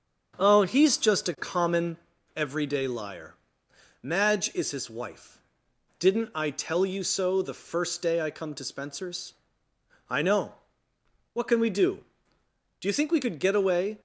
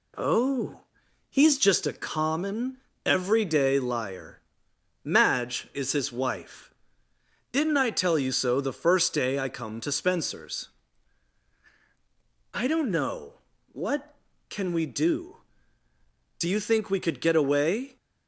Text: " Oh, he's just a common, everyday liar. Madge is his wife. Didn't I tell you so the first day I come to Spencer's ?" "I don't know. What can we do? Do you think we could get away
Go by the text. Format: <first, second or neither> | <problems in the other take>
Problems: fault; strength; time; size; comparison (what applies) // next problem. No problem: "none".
second | starts louder than the rest; strong; until 1.3 s; 7 dB // skips "don't"; at 10.2 s